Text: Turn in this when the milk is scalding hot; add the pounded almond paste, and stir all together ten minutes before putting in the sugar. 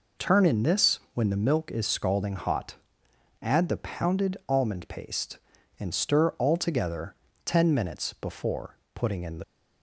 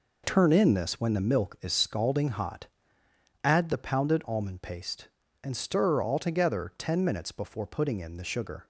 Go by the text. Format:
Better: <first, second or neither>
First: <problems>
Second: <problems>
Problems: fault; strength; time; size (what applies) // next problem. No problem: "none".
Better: second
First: pauses between "this" and "when"; slight; at 0.9 s; 0.16 s long // pauses between "together" and "ten"; slight; at 7.1 s; 0.30 s long // pauses between "before" and "putting"; slight; at 8.7 s; 0.18 s long // stops before "sugar"; at 9.4 s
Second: none